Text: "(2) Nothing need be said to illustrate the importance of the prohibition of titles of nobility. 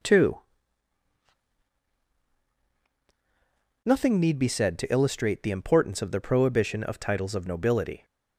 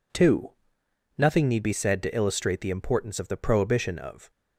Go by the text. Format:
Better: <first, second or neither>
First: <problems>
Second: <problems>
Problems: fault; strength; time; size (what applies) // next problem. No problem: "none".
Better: first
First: none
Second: stops before "titles of nobility"; at 4.3 s